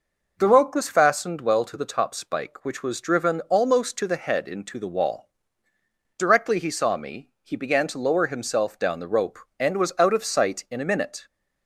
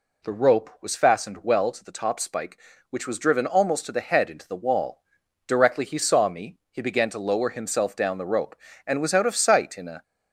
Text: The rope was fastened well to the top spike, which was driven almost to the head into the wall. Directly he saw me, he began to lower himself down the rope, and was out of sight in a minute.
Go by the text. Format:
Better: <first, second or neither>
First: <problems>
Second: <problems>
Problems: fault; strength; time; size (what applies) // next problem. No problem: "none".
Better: first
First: none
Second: stops before "minute"; at 10.0 s